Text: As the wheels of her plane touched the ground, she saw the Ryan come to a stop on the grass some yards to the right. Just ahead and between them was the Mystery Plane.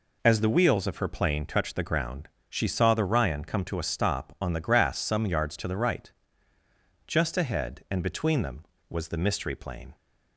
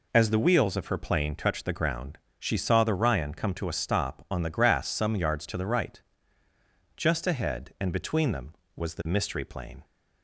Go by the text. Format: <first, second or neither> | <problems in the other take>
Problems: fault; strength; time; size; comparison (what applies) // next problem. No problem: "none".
neither | none